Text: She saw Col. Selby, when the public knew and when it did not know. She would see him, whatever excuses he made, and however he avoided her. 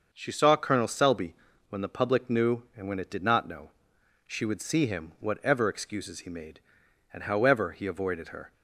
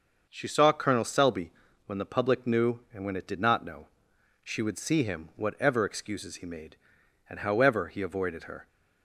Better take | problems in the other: neither | starts louder than the rest; the same in both

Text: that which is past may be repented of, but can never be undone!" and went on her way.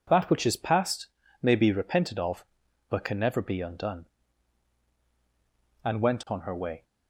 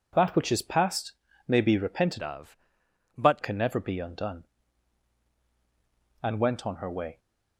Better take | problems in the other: first | pauses between "past" and "may"; slight; at 1.1 s; 0.36 s long; slight in the first // changes voice from "of" to "but"; from 2.2 to 3.4 s; 1.2 s long

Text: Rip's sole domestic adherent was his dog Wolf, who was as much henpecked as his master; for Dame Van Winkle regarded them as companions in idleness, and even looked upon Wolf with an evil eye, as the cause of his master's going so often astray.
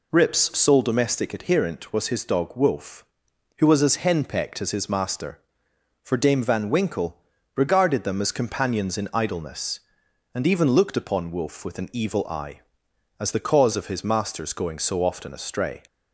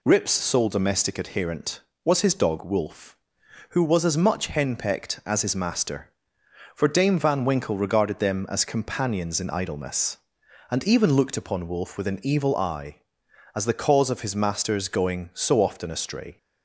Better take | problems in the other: second | skips "much"; at 3.9 s // pauses between "Winkle" and "regarded"; at 7.1 s; 0.38 s long

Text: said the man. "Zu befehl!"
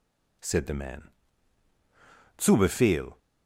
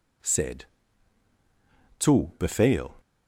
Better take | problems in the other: first | skips "the man"; at 1.3 s

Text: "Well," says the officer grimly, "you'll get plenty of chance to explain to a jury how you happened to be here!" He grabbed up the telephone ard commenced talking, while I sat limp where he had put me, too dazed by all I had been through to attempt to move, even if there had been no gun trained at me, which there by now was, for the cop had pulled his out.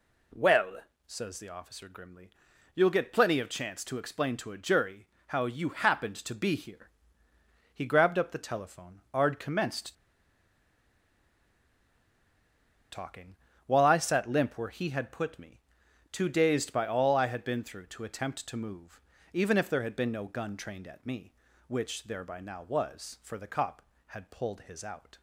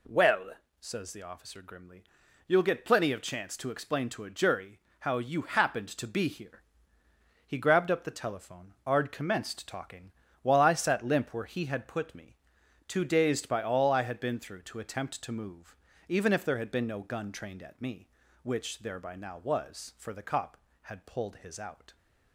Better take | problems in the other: second | pauses between "jury" and "how"; slight; at 5.0 s; 0.20 s long; slight in the second // pauses between "commenced" and "talking"; strong; at 9.9 s; 2.9 s long

